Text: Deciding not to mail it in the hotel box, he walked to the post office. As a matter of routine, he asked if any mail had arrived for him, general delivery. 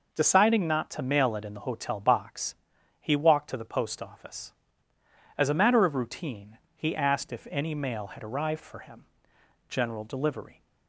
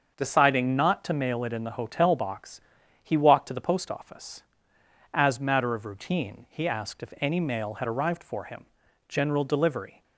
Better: first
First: none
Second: starts louder than the rest; until 1.1 s; 6.5 dB // skips "a"; at 5.4 s

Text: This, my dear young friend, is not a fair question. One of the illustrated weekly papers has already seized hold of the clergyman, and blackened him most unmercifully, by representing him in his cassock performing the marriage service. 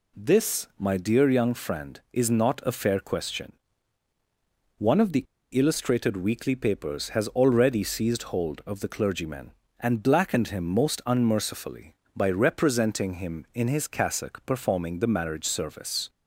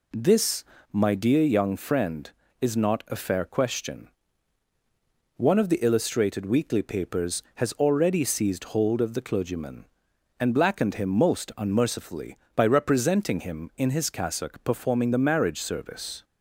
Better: second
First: pauses between "the" and "illustrated"; slight; at 5.2 s; 0.28 s long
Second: none

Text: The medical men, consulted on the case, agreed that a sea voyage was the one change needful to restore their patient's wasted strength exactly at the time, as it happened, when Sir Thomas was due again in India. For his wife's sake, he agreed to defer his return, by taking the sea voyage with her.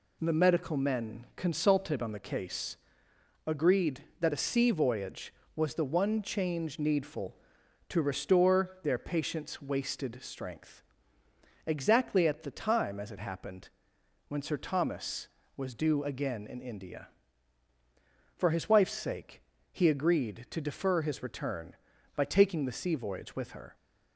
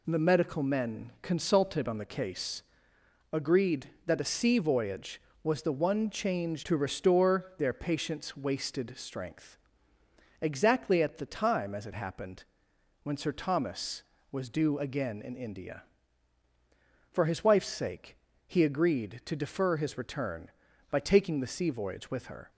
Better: first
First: pauses between "strength" and "exactly"; noticeable; at 10.8 s; 0.86 s long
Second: skips "needful"; at 6.6 s // pauses between "strength" and "exactly"; noticeable; at 9.5 s; 0.86 s long

